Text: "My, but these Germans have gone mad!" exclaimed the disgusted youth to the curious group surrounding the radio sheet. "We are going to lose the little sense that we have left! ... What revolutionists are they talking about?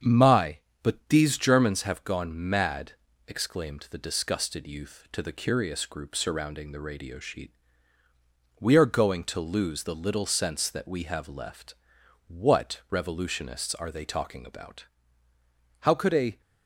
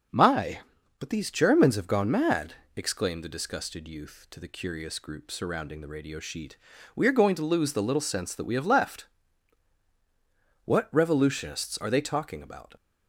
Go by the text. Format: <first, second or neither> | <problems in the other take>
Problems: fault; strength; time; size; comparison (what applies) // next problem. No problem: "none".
second | starts louder than the rest; strong; until 1.3 s; 7.5 dB; also in the second // pauses between "gone" and "mad"; slight; at 2.3 s; 0.16 s long // goes on to say "How could a"; from 15.8 s on; 0.60 s long